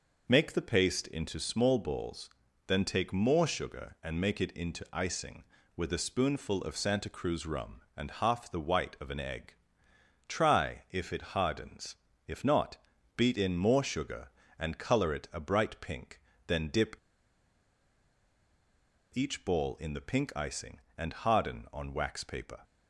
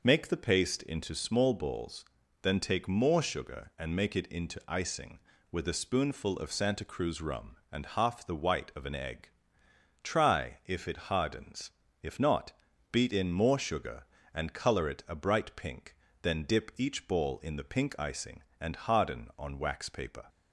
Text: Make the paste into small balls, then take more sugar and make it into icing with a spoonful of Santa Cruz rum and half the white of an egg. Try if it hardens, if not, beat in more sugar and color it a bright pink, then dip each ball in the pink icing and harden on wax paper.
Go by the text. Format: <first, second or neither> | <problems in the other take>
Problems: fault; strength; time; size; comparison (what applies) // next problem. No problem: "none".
second | pauses between "dip" and "each"; strong; at 16.9 s; 2.1 s long